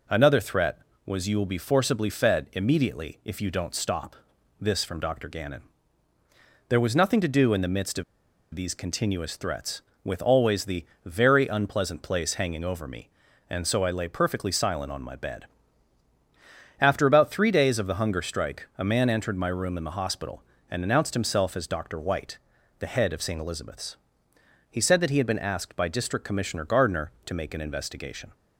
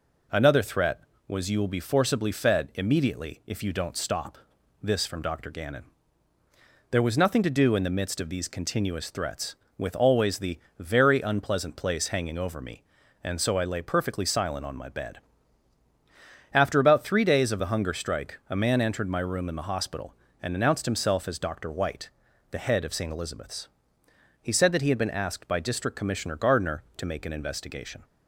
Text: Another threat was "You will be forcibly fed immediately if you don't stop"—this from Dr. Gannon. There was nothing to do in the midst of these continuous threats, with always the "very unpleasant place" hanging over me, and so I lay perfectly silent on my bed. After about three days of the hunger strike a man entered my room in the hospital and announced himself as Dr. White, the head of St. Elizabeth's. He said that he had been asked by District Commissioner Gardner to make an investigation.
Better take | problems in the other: second | pauses between "of" and "these"; noticeable; at 8.0 s; 0.50 s long // pauses between "the" and "very"; slight; at 10.8 s; 0.20 s long; slight in the second

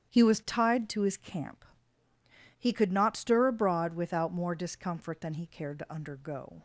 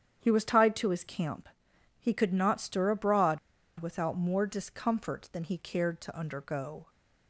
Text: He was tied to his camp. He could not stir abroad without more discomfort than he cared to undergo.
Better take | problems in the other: first | starts louder than the rest; strong; until 1.2 s; 9 dB; strong in the first // pauses between "abroad" and "without"; at 3.3 s; 0.41 s long

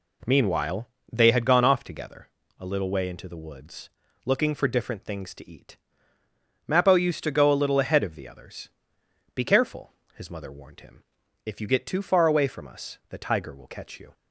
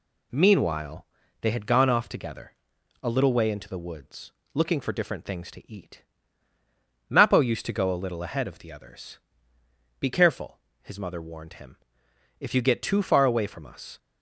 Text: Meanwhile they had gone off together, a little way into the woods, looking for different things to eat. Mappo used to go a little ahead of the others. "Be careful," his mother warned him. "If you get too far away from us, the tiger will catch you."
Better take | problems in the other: first | pauses between "Meanwhile" and "they"; slight; at 1.0 s; 0.36 s long; slight in the first // stops before "the tiger will catch you"; at 13.9 s

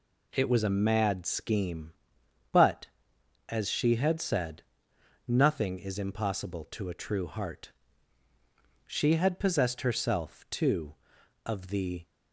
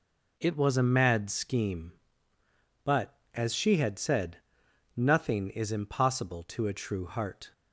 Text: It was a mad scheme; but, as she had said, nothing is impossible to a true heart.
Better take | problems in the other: second | goes on to say "She had possessed herself too of the"; strong; from 8.8 s on; 3.1 s long

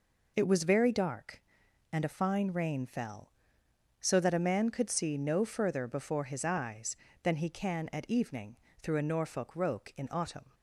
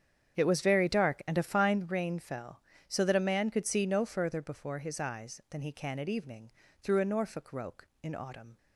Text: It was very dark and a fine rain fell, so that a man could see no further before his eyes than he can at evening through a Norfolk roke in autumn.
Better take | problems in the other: first | starts louder than the rest; strong; until 1.9 s; 8 dB // pauses between "evening" and "through"; slight; at 6.5 s; 0.30 s long; slight in the first

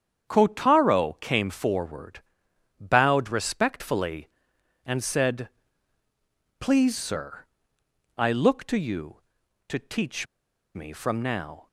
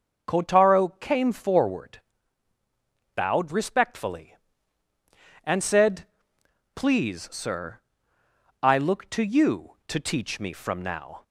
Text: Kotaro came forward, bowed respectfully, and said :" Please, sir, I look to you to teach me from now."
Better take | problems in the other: second | starts louder than the rest; strong; until 1.3 s; 8.5 dB; also in the second // pauses between "teach" and "me"; noticeable; at 10.2 s; 0.49 s long

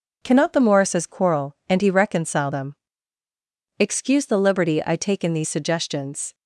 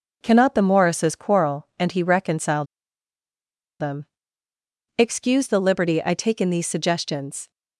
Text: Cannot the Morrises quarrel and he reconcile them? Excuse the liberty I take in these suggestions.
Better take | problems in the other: first | pauses between "reconcile" and "them"; at 2.6 s; 1.1 s long

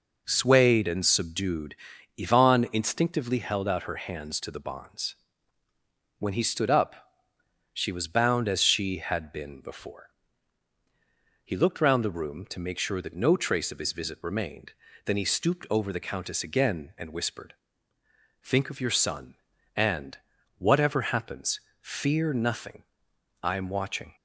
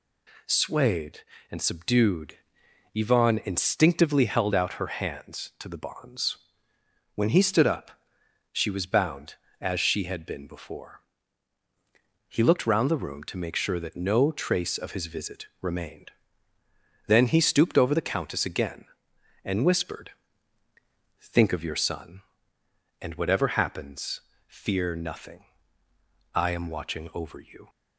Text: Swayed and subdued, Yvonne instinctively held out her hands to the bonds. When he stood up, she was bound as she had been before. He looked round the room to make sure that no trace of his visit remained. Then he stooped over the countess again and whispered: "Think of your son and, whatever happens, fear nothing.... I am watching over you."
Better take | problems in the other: second | stops before "over you"; at 24.1 s

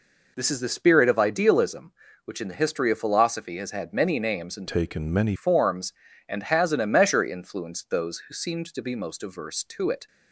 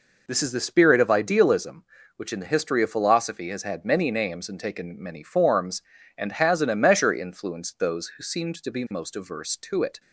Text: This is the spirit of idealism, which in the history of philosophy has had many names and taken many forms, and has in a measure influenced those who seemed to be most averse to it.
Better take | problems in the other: second | changes voice from "taken" to "many"; from 4.6 to 5.3 s; 0.7 s long

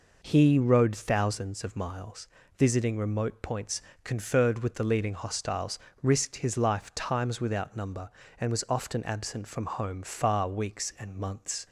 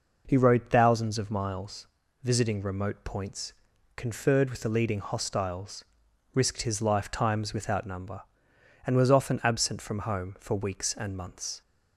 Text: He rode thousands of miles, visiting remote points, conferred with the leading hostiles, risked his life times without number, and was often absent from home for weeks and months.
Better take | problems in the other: second | says "far" for "for"; at 10.0 s

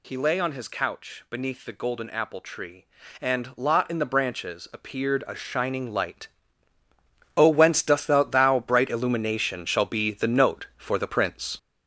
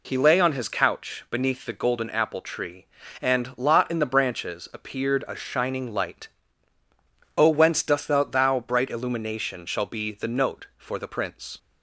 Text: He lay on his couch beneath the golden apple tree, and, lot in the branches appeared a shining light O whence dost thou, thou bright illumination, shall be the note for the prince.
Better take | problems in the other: second | gets louder; noticeable; throughout; 5.5 dB // pauses between "light" and "O"; at 6.2 s; 1.0 s long; also in the second

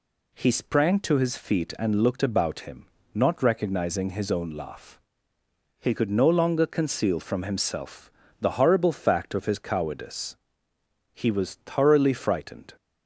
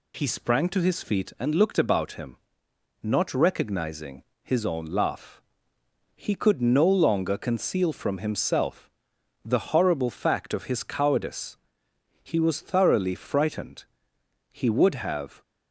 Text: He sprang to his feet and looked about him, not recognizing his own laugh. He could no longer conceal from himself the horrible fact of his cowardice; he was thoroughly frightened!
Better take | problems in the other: first | pauses between "recognizing" and "his"; slight; at 4.2 s; 0.20 s long // pauses between "himself" and "the"; noticeable; at 8.9 s; 0.52 s long; slight in the first // goes on to say "He would have"; noticeable; from 14.5 s on; 0.90 s long

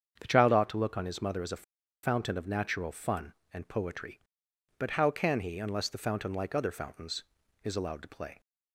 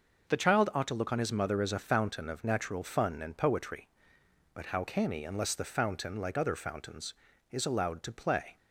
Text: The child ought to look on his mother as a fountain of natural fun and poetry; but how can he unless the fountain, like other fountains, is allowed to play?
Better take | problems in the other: second | starts louder than the rest; strong; until 1.2 s; 7.5 dB // pauses between "a" and "fountain"; at 1.6 s; 0.41 s long

